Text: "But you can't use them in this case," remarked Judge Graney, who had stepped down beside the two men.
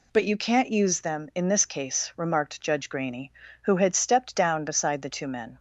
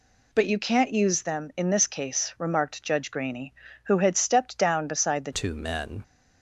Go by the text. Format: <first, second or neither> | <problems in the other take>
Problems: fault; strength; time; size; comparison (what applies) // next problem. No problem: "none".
first | changes voice at "two"; from 5.3 s on; 0.7 s long